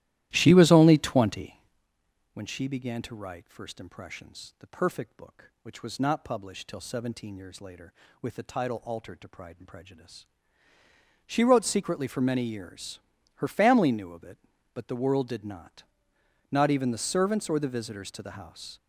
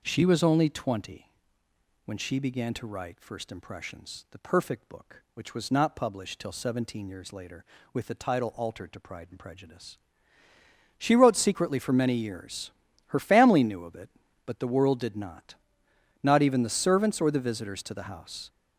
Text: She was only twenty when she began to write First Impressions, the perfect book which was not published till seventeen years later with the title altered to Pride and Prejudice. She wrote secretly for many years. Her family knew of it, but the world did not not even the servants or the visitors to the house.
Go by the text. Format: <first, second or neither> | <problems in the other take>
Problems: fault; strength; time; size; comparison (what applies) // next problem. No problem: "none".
second | starts louder than the rest; strong; until 1.9 s; 14.5 dB // pauses between "twenty" and "when"; noticeable; at 1.5 s; 0.74 s long; noticeable in the second // pauses between "not" and "not"; noticeable; at 15.8 s; 0.66 s long; noticeable in the second